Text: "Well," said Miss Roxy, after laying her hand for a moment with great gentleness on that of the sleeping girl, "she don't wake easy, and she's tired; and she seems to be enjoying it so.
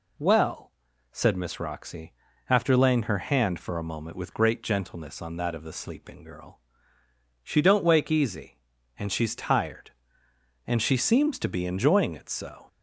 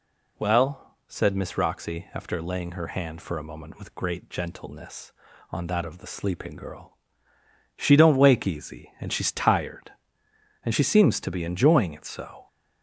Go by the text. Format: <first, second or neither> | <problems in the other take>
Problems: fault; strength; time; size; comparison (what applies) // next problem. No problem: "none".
neither | none